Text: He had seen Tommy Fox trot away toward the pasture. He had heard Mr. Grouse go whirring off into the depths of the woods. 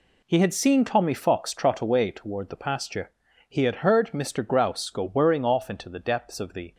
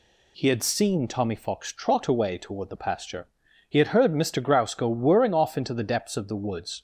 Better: second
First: stops before "woods"; at 6.7 s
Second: none

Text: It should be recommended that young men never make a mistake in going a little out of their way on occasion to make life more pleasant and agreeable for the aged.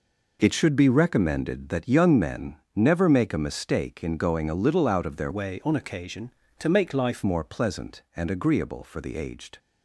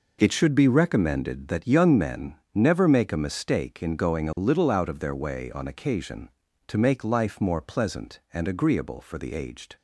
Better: second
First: pauses between "men" and "never"; slight; at 2.5 s; 0.18 s long // changes voice from "way" to "life"; from 5.3 to 7.2 s; 1.9 s long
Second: pauses between "men" and "never"; slight; at 2.3 s; 0.18 s long

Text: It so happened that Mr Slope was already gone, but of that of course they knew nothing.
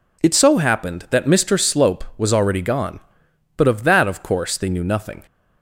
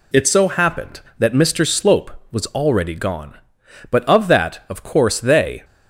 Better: first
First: none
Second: stops before "knew nothing"; at 5.6 s

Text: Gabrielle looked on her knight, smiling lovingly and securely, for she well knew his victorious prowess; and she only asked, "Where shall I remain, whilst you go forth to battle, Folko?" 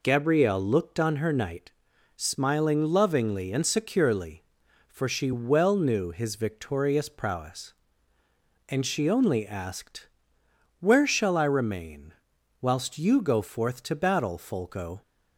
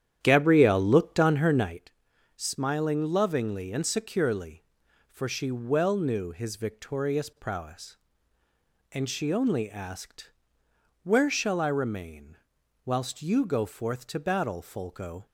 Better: first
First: none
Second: starts louder than the rest; strong; until 1.8 s; 10 dB

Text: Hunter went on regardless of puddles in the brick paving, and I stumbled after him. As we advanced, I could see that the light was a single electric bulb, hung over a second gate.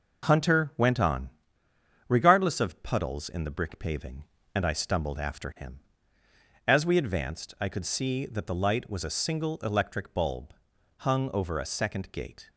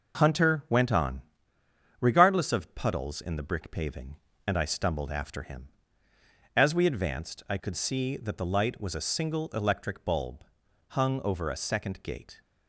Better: neither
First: pauses between "on" and "regardless"; noticeable; at 1.2 s; 0.80 s long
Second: pauses between "on" and "regardless"; noticeable; at 1.1 s; 0.80 s long

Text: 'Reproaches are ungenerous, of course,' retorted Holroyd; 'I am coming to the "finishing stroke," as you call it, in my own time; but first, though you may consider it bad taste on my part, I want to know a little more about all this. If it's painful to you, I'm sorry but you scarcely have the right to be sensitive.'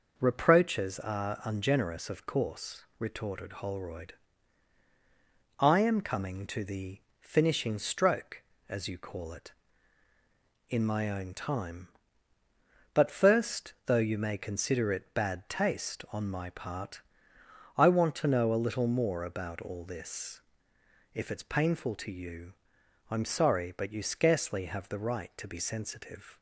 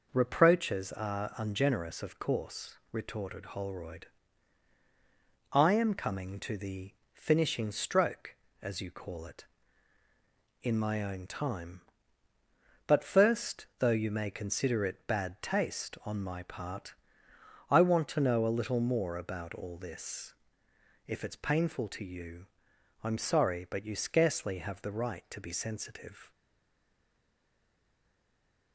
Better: first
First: pauses between "the" and "finishing"; slight; at 7.0 s; 0.18 s long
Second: pauses between "the" and "finishing"; slight; at 6.9 s; 0.18 s long // stays silent after the last word; from 26.3 s on; 2.4 s long

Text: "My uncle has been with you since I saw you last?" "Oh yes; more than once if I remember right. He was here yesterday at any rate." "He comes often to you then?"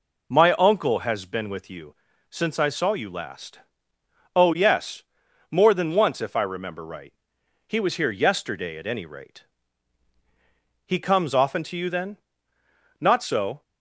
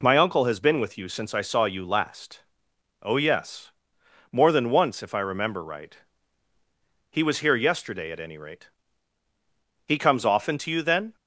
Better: second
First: pauses between "you" and "since"; slight; at 1.9 s; 0.34 s long // goes on to say "Not so"; noticeable; from 12.9 s on; 0.62 s long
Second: none

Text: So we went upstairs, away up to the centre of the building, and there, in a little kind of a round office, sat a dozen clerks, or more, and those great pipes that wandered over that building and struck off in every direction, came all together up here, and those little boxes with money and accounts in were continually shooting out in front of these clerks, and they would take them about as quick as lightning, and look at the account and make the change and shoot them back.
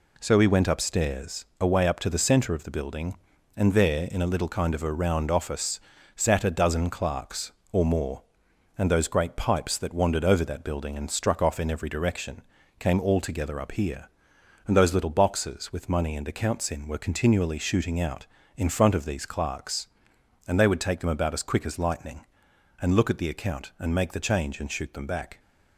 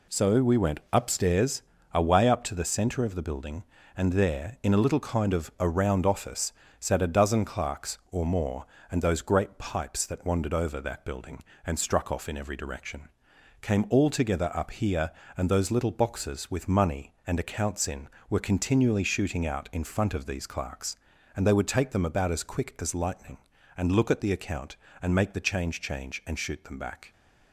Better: first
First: none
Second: says "change" twice; at 25.8 s

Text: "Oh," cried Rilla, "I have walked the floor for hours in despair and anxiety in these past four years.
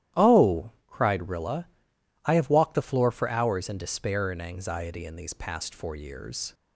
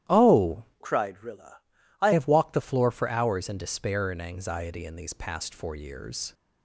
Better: first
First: starts louder than the rest; strong; until 1.3 s; 12.5 dB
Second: starts louder than the rest; strong; until 1.2 s; 12 dB // changes voice from "cried" to "I"; from 0.8 to 2.1 s; 1.3 s long

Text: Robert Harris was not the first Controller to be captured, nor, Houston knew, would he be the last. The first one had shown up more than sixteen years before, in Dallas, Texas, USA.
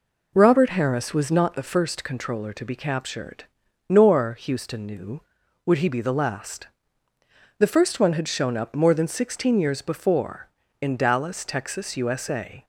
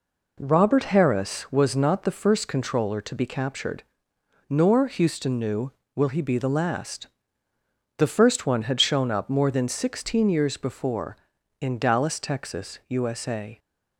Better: first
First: none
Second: says "will" for "would"; at 5.9 s

